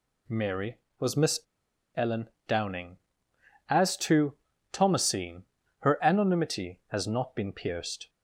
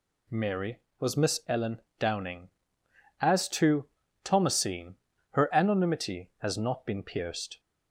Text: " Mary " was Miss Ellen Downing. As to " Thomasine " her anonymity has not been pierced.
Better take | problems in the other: second | pauses between "Miss" and "Ellen"; noticeable; at 1.3 s; 0.56 s long // pauses between "Ellen" and "Downing"; slight; at 2.2 s; 0.20 s long; slight in the second

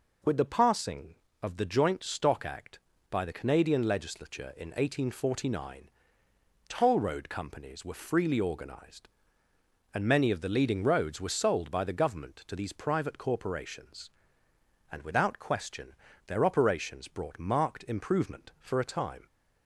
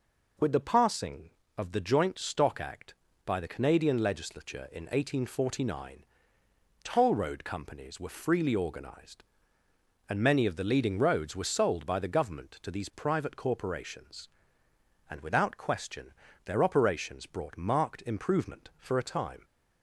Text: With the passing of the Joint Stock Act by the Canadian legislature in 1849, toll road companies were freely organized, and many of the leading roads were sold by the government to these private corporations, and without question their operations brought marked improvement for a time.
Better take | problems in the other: neither | pauses between "question" and "their"; slight; the same in both

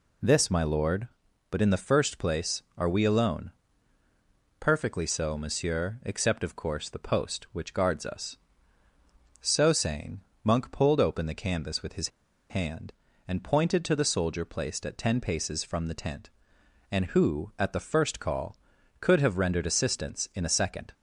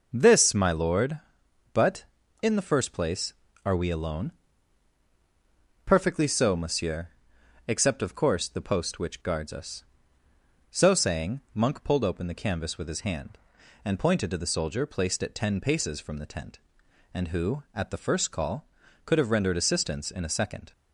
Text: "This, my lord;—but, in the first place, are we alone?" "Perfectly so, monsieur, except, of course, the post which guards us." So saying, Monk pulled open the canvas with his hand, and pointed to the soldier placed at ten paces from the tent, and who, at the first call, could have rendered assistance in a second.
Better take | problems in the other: second | pauses between "his" and "hand"; at 12.0 s; 0.41 s long

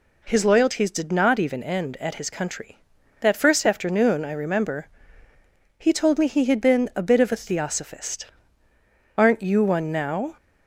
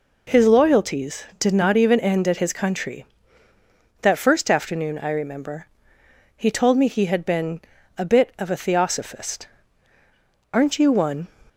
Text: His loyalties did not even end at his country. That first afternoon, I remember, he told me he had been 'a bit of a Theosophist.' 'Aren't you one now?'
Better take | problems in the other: first | pauses between "been" and "a"; slight; at 7.6 s; 0.34 s long // stops before "now"; at 11.4 s

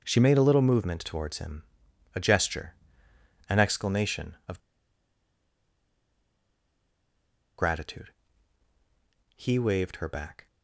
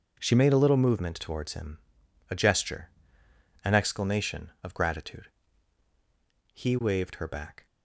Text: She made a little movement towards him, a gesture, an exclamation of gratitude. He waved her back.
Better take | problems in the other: second | pauses between "of" and "gratitude"; strong; at 4.5 s; 2.9 s long

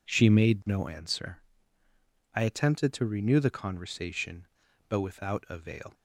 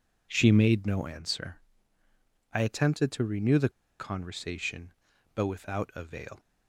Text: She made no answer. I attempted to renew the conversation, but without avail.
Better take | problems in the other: first | pauses between "the" and "conversation"; slight; at 3.6 s; 0.29 s long

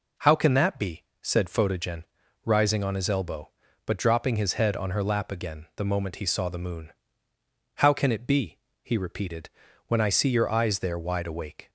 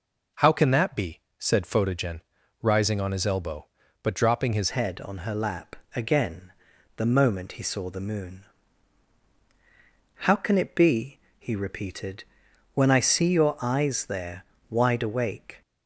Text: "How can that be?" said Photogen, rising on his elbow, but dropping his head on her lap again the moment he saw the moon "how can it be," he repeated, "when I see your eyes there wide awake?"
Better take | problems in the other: first | changes voice at "head"; from 4.7 s on; 10.9 s long // pauses between "lap" and "again"; slight; at 5.7 s; 0.20 s long // pauses between "again" and "the"; noticeable; at 6.5 s; 0.46 s long // pauses between "moon" and "how"; strong; at 8.4 s; 1.7 s long; noticeable in the first // pauses between "there" and "wide"; slight; at 14.4 s; 0.26 s long

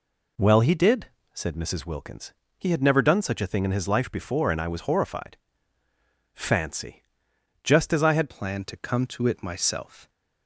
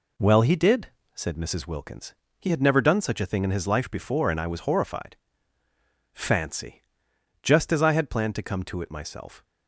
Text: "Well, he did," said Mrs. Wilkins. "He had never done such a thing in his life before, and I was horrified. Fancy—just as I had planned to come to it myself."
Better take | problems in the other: second | changes voice at "planned"; from 8.2 s on; 1.8 s long

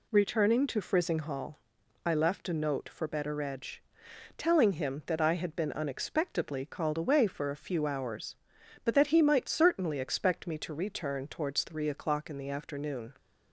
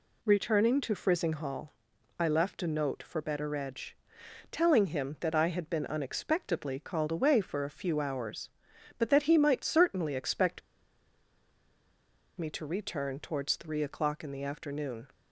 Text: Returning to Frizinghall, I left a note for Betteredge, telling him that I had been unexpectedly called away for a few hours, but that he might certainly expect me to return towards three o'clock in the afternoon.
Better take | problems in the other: first | pauses between "expect" and "me"; strong; at 10.6 s; 1.7 s long

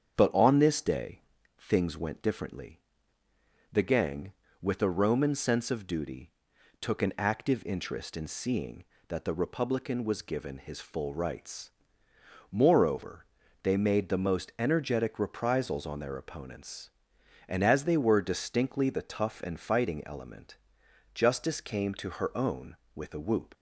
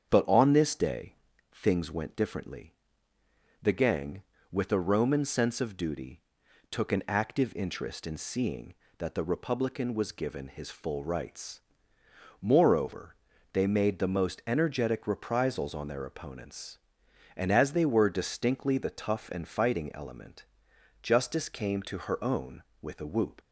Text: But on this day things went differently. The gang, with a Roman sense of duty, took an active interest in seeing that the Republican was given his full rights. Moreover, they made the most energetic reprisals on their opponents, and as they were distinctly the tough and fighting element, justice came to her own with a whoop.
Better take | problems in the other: neither | starts louder than the rest; strong; the same in both // pauses between "day" and "things"; the same in both

